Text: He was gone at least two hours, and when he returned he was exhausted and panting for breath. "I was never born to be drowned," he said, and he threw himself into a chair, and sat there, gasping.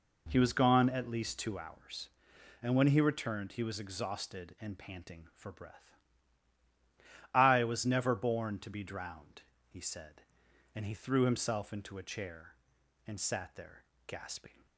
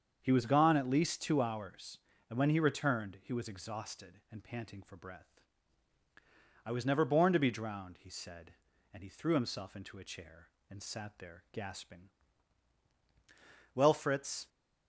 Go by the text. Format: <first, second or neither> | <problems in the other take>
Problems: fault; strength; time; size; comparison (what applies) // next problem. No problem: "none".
first | starts louder than the rest; strong; until 1.2 s; 7 dB // goes on to say "Well Fritz"; noticeable; from 13.7 s on; 0.74 s long